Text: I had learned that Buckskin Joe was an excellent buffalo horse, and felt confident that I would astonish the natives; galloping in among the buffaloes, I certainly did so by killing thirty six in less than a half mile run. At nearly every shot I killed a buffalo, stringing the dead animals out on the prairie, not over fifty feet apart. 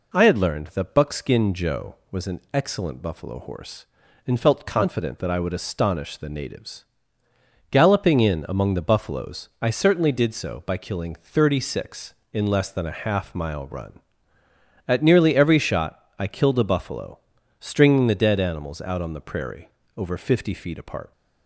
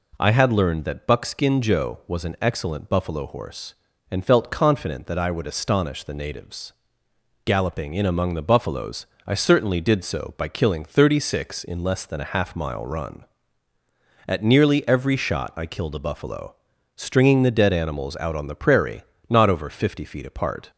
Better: second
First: pauses between "shot" and "I"; slight; at 16.0 s; 0.16 s long // skips "not"; at 19.8 s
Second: none

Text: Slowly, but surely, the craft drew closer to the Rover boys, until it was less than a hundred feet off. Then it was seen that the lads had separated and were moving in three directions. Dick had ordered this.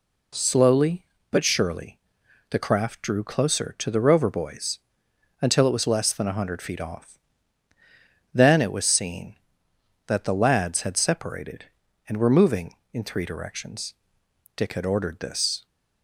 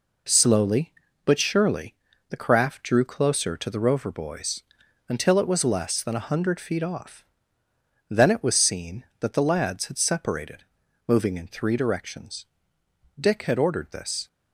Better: first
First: none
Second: skips "and were"; at 10.8 s

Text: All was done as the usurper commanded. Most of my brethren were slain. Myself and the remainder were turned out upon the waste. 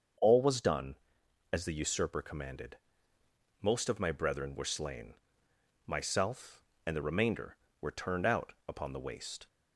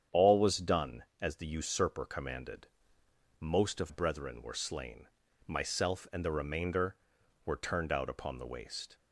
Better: first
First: starts louder than the rest; until 1.7 s; 6.5 dB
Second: starts louder than the rest; strong; until 1.3 s; 8.5 dB // skips "my"; at 3.8 s

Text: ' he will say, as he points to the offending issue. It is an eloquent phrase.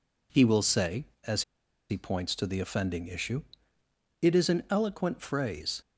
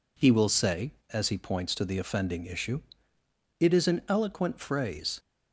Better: second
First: pauses between "as" and "he"; noticeable; at 1.4 s; 0.46 s long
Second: none

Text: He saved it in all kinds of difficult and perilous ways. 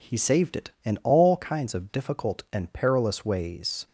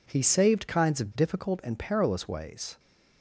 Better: first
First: none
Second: skips "it in all"; at 0.6 s

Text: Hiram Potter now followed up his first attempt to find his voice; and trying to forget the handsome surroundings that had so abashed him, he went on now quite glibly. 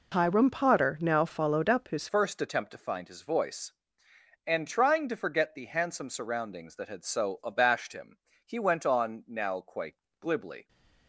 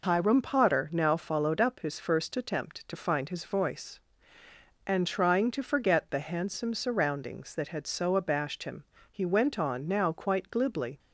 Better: second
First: changes voice at "first"; from 2.0 s on; 8.6 s long // pauses between "quite" and "glibly"; slight; at 9.9 s; 0.24 s long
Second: none

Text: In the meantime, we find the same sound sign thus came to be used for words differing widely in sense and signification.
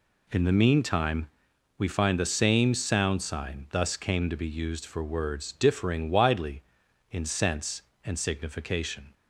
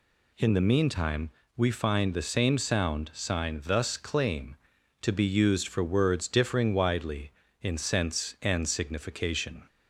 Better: first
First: none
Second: says "claim" for "came"; at 3.9 s

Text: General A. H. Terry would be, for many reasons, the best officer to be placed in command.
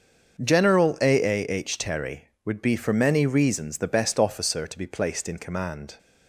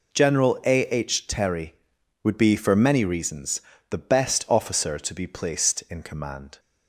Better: second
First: says "A" twice; at 1.2 s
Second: none

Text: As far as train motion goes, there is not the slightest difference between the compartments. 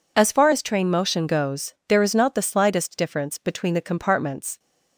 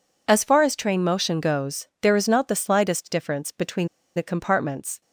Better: first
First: none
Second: pauses between "between" and "the"; slight; at 3.8 s; 0.28 s long

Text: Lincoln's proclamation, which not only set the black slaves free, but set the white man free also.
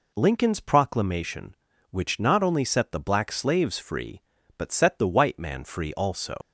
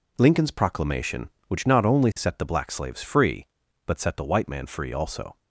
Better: second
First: leaves "also" unfinished; at 6.4 s; 85 ms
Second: none

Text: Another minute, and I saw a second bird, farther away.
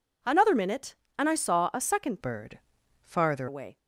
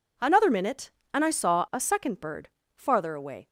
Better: second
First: changes voice from "bird" to "farther"; from 2.2 to 3.4 s; 1.2 s long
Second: none

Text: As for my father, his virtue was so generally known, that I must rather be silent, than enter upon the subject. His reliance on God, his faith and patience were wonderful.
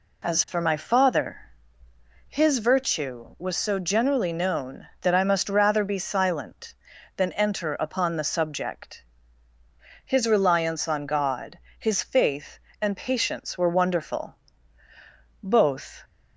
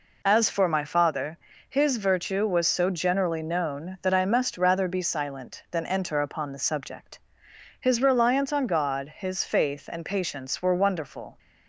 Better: second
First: goes on to say "Both"; noticeable; from 15.4 s on; 0.62 s long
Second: none

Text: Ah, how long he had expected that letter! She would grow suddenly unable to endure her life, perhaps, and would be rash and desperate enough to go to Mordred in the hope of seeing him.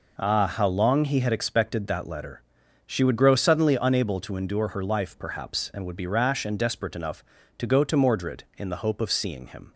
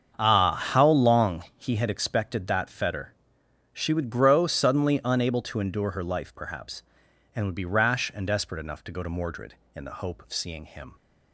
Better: first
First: none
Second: starts louder than the rest; strong; until 1.2 s; 7 dB // says "fetter" for "letter"; at 2.6 s

